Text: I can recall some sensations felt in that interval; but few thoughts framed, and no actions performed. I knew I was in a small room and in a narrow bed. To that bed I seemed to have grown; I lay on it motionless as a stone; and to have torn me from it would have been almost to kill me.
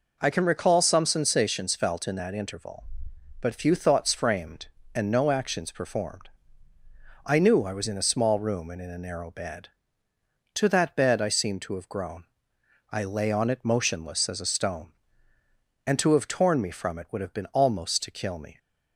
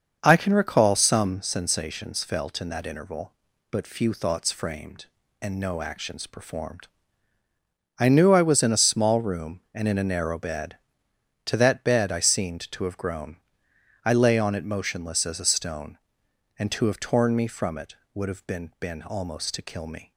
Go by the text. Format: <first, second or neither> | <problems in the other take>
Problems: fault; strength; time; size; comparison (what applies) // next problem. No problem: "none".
first | starts louder than the rest; until 1.2 s; 6.5 dB // says "been" twice; at 18.7 s